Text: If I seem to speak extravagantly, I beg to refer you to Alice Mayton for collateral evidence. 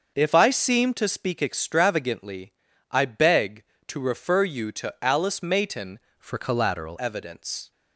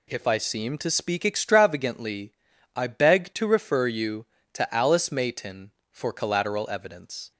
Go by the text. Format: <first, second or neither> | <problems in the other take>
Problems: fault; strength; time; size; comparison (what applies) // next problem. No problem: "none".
second | starts louder than the rest; until 1.1 s; 6 dB // changes voice from "for" to "collateral"; from 6.1 to 6.9 s; 0.8 s long